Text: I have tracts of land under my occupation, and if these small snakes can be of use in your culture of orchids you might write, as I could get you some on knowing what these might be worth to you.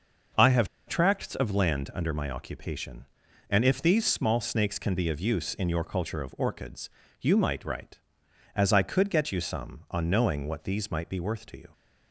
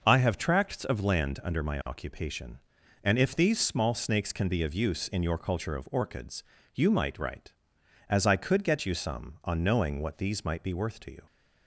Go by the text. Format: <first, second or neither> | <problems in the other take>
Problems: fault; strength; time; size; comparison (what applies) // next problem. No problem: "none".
second | pauses between "have" and "tracts"; slight; at 0.6 s; 0.20 s long // pauses between "orchids" and "you"; slight; at 6.8 s; 0.32 s long; slight in the second